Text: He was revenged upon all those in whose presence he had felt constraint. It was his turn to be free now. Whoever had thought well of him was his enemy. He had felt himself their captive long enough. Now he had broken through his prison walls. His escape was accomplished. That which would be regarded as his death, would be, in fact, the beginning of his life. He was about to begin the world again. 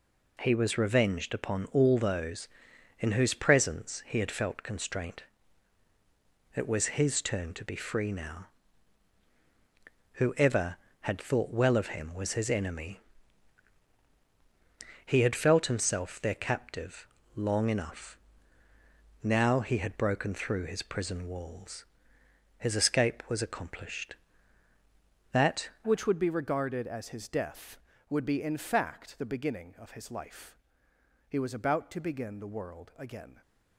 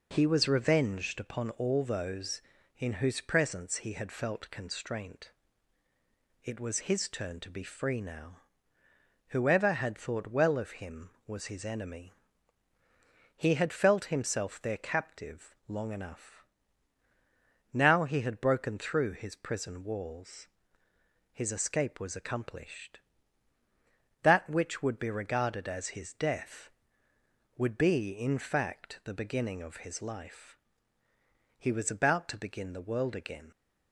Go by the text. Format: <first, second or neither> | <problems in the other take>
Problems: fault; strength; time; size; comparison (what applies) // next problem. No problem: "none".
second | pauses between "captive" and "long"; slight; at 17.0 s; 0.30 s long // changes voice at "which"; from 25.8 s on; 7.6 s long